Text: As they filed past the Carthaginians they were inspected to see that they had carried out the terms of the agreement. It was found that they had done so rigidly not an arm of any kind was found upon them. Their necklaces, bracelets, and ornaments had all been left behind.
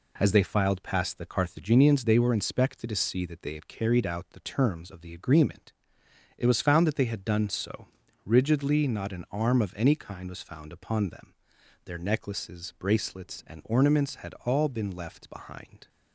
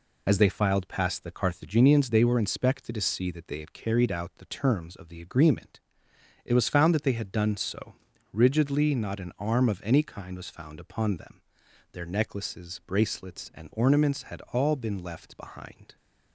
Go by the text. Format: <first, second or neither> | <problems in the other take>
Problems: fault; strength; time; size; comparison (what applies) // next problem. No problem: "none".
first | loses the start of "As"; at 0.2 s; 55 ms // pauses between "so" and "rigidly"; slight; at 7.9 s; 0.36 s long; slight in the first